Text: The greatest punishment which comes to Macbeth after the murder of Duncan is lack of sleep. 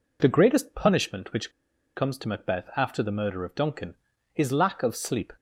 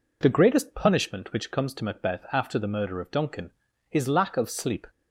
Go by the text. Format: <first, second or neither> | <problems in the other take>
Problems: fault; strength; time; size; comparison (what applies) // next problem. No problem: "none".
second | pauses between "which" and "comes"; noticeable; at 1.4 s; 0.46 s long